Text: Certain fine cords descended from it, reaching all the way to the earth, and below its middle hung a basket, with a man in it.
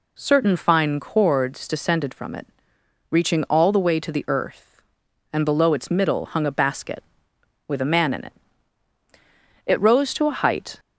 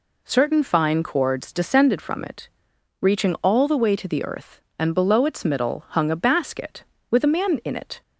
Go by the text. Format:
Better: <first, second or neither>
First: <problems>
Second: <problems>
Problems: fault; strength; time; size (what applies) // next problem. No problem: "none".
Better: second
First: goes on to say "It rose to a height"; noticeable; from 9.6 s on; 1.1 s long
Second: none